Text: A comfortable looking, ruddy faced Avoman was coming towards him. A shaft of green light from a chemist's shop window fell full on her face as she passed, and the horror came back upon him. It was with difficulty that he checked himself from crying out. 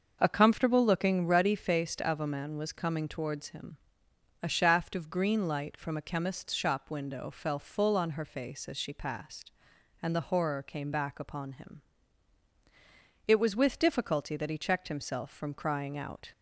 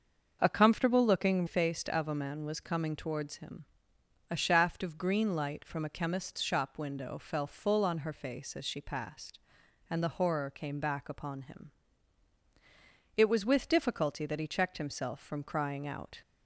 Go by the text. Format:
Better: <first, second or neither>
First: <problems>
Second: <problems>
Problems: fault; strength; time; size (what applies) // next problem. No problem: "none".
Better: first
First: starts louder than the rest; until 1.2 s; 6.5 dB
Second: starts louder than the rest; until 1.4 s; 6.5 dB // skips "ruddy"; at 1.4 s